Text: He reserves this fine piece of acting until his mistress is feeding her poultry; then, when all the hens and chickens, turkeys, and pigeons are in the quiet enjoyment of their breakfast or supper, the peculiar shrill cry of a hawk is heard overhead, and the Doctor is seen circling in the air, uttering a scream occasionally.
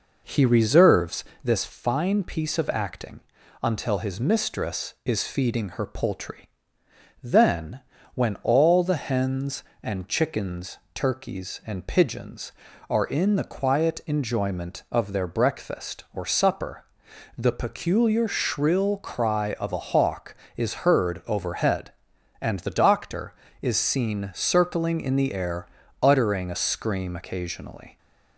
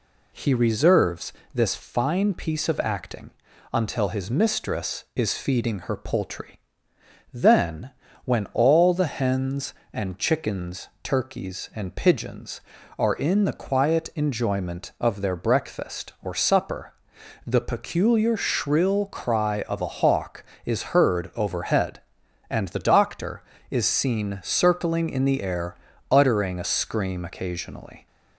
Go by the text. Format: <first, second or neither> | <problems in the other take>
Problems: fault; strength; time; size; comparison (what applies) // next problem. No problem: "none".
second | starts louder than the rest; noticeable; until 1.5 s; 5 dB // pauses between "reserves" and "this"; slight; at 1.2 s; 0.20 s long; slight in the second // pauses between "acting" and "until"; at 3.1 s; 0.42 s long; also in the second